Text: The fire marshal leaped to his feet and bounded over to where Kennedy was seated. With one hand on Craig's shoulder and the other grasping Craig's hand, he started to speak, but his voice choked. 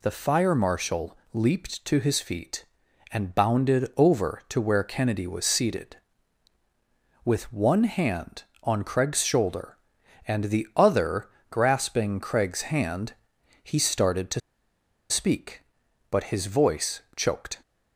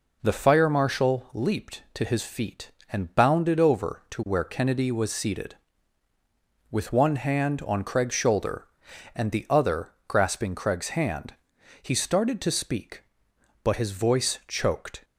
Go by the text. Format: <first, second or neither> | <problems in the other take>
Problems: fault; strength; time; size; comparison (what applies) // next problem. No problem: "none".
second | pauses between "marshal" and "leaped"; slight; at 1.1 s; 0.18 s long // pauses between "other" and "grasping"; slight; at 11.2 s; 0.22 s long; slight in the second // pauses between "to" and "speak"; noticeable; at 14.4 s; 0.70 s long // pauses between "voice" and "choked"; slight; at 17.0 s; 0.16 s long